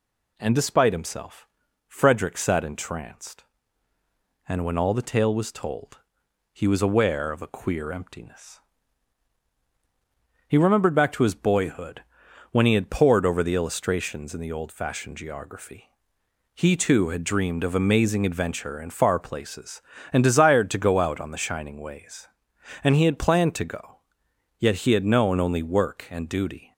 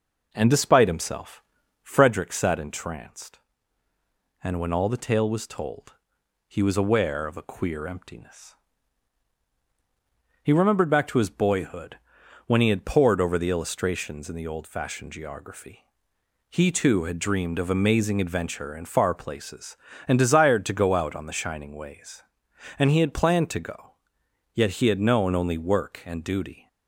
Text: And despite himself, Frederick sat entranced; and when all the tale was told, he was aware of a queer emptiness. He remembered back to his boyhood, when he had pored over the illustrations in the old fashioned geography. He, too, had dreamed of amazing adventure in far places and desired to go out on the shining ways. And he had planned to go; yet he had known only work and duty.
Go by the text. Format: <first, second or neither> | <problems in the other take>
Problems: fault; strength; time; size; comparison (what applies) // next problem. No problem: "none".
first | starts louder than the rest; noticeable; until 2.2 s; 5 dB